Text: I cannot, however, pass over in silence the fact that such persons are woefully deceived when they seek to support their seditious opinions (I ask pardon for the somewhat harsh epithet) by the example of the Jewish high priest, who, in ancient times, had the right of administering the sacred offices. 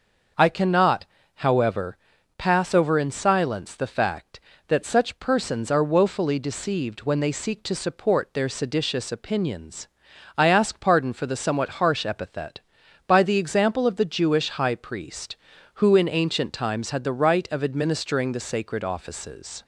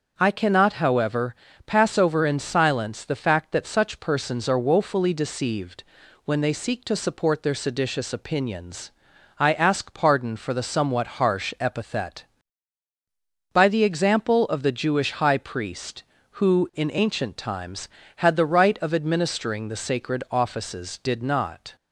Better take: first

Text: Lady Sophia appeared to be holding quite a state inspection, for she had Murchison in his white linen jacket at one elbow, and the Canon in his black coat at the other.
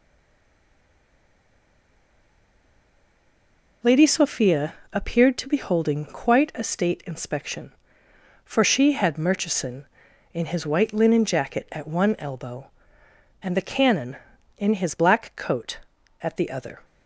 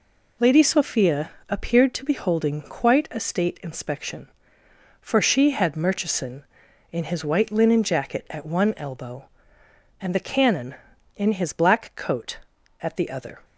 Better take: second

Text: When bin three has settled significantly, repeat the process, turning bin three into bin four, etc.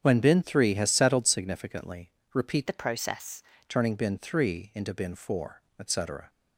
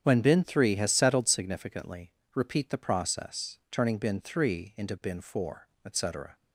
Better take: second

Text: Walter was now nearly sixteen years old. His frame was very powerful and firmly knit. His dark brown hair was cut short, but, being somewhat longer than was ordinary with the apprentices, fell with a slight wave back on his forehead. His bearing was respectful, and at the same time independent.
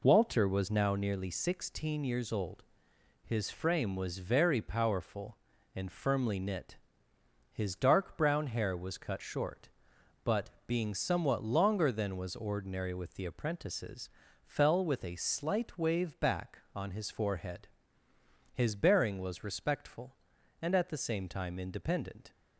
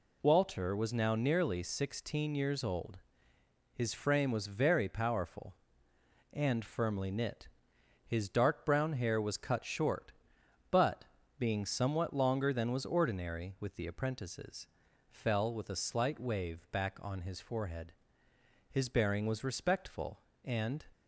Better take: first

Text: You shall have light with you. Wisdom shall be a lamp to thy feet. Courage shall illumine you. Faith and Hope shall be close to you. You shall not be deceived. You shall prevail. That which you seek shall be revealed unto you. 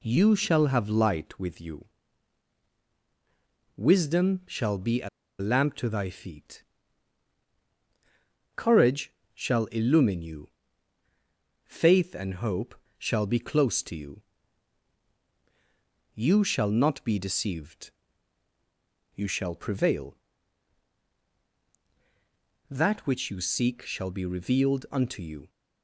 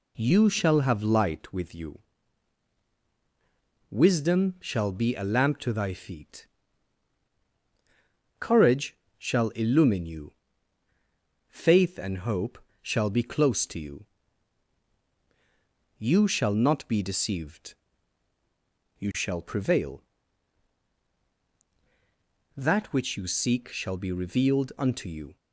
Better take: second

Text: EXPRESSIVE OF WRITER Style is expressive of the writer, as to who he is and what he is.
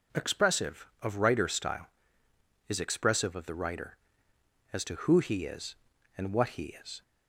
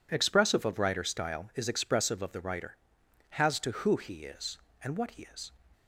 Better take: first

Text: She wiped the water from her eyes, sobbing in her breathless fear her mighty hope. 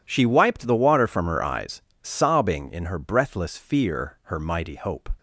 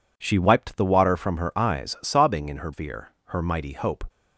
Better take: first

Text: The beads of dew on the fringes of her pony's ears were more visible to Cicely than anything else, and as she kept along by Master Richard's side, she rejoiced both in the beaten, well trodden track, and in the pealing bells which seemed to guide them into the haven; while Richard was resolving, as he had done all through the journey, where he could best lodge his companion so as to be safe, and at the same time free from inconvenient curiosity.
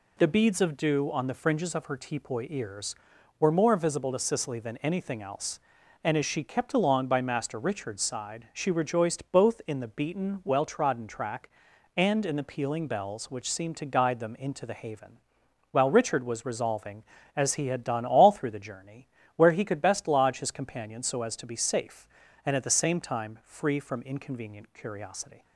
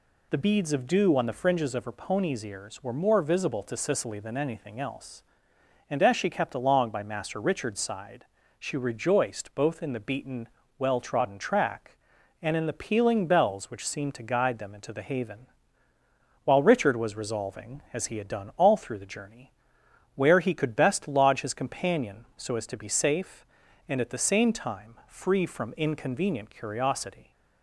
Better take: second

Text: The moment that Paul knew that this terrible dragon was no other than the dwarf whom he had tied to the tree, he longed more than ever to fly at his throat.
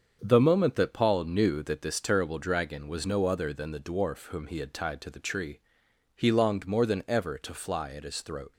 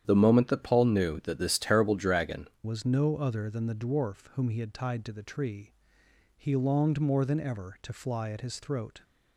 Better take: first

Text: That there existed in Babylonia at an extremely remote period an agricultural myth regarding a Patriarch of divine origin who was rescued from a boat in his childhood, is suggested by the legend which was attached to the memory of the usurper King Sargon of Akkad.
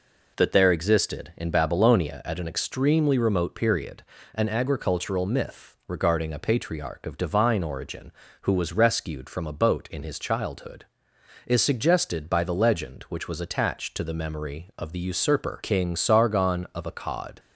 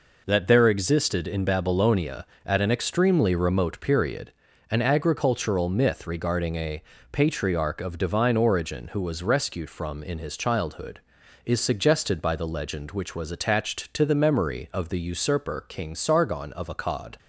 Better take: first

